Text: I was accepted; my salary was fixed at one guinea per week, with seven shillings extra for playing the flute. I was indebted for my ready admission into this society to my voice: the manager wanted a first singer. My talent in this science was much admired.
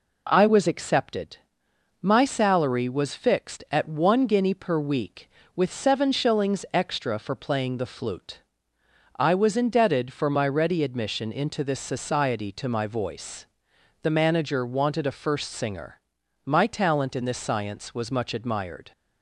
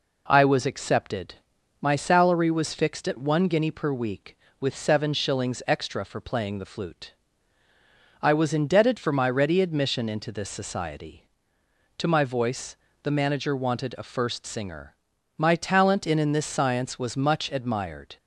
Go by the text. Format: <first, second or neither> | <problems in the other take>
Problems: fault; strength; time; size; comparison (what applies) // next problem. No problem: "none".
first | says "in" twice; at 16.1 s